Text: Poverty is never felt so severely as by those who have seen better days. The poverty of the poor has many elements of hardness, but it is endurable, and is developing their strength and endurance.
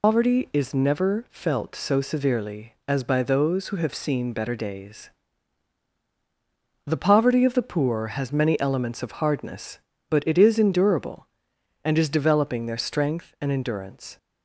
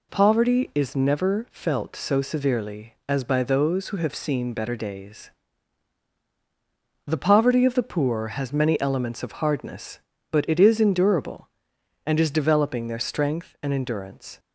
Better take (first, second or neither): second